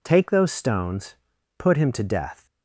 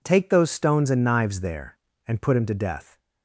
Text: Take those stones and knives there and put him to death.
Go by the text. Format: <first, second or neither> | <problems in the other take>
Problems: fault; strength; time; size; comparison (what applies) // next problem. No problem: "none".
second | skips "and knives there and"; at 1.3 s